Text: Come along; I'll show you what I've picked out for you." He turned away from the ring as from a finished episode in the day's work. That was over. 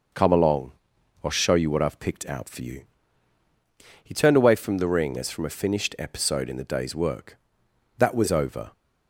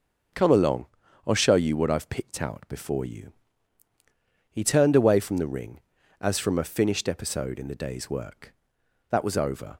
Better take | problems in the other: first | says "before" for "for"; at 2.6 s

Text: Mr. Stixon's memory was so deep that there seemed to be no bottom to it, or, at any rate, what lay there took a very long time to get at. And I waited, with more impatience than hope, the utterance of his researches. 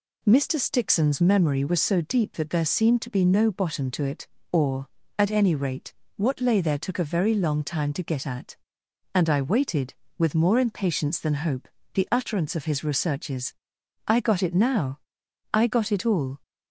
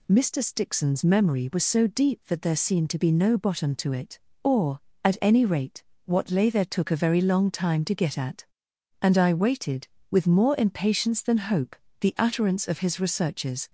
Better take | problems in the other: second | goes on to say "I got it now I got it all"; strong; from 14.0 s on; 2.3 s long

